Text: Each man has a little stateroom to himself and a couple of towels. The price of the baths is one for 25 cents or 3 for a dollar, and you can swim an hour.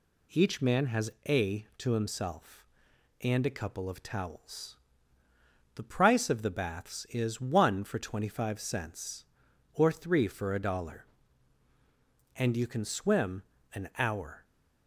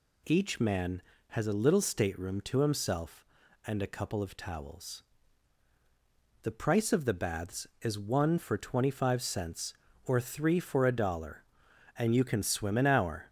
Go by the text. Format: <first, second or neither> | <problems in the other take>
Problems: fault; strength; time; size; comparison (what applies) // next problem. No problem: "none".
second | pauses between "has" and "a"; slight; at 1.1 s; 0.16 s long // skips "little stateroom"; at 1.7 s // pauses between "swim" and "an"; slight; at 13.4 s; 0.30 s long